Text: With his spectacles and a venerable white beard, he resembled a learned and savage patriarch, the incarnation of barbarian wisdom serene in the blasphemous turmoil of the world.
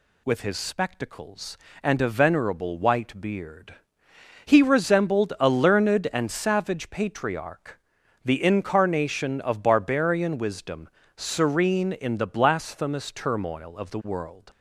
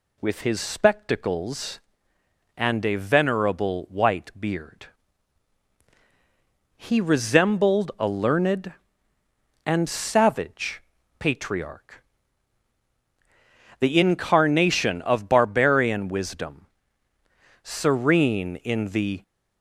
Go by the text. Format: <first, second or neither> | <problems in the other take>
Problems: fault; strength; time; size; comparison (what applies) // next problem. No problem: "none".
first | pauses between "savage" and "patriarch"; at 10.8 s; 0.38 s long // pauses between "wisdom" and "serene"; noticeable; at 16.6 s; 0.98 s long; slight in the first // stops before "blasphemous turmoil of the world"; at 19.2 s